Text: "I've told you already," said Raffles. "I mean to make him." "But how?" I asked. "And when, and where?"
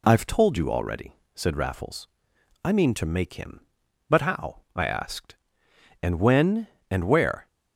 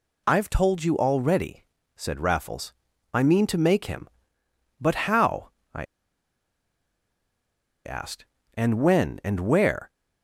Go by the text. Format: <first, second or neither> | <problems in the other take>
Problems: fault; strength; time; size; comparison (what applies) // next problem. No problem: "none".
first | pauses between "I" and "asked"; strong; at 5.8 s; 2.0 s long